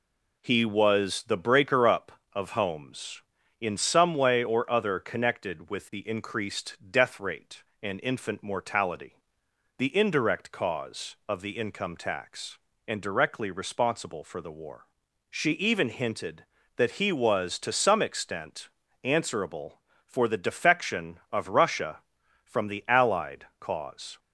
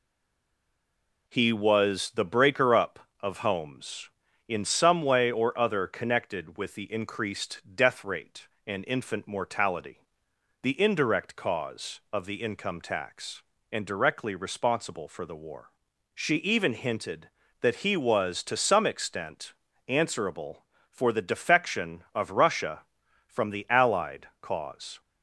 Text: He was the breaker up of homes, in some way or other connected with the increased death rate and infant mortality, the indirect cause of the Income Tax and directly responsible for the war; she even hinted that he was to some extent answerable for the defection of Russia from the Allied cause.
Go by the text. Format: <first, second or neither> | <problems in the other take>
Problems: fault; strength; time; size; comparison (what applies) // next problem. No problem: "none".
first | stays silent before the first word; noticeable; until 1.2 s; 1.2 s long // pauses between "extent" and "answerable"; slight; at 19.5 s; 0.36 s long; slight in the first